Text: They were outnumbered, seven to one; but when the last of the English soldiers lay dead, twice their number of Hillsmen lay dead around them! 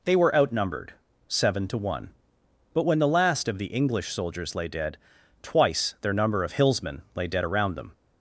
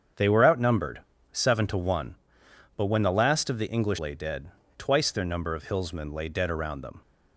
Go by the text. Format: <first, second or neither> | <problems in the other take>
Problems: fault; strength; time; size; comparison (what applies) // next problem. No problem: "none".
first | starts louder than the rest; strong; until 1.4 s; 7.5 dB // skips "soldiers"; at 3.9 s